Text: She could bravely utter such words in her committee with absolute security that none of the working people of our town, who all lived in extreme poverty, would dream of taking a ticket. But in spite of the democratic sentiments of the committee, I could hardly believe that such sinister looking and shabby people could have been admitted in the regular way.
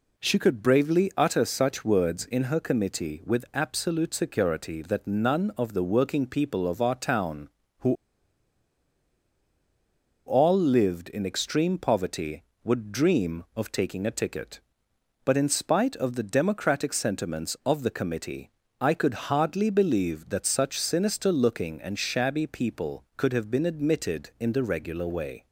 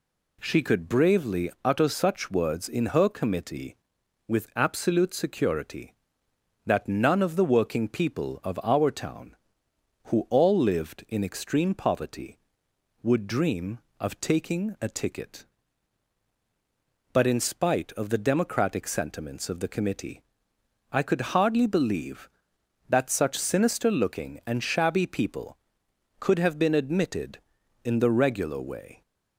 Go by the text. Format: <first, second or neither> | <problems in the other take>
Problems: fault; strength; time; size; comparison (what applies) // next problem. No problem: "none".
second | pauses between "who" and "all"; strong; at 7.9 s; 2.3 s long